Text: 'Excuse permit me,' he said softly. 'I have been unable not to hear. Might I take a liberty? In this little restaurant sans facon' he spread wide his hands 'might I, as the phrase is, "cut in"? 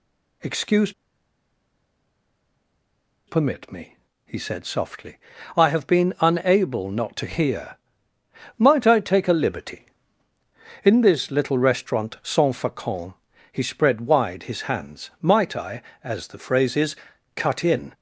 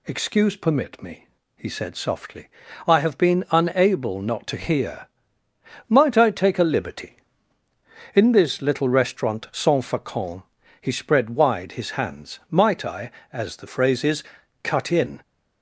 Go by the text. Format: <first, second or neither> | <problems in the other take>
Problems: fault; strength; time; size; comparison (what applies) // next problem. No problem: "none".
second | pauses between "Excuse" and "permit"; strong; at 0.9 s; 2.3 s long // pauses between "facon" and "he"; slight; at 13.1 s; 0.36 s long; slight in the second